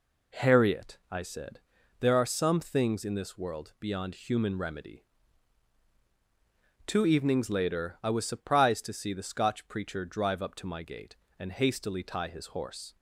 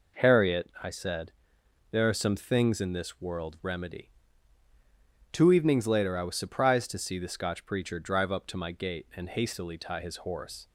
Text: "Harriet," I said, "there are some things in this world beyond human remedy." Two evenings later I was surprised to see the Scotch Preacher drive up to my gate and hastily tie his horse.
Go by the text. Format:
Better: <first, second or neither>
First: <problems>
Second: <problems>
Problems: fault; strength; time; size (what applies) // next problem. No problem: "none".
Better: first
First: none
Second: skips "beyond human"; at 3.6 s